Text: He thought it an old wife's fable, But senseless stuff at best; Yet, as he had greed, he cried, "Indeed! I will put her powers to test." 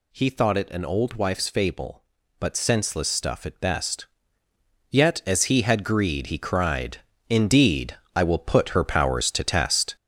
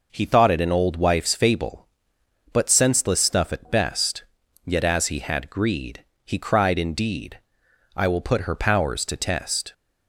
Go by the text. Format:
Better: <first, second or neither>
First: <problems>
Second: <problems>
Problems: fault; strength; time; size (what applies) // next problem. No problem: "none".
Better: second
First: gets louder; throughout; 7 dB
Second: none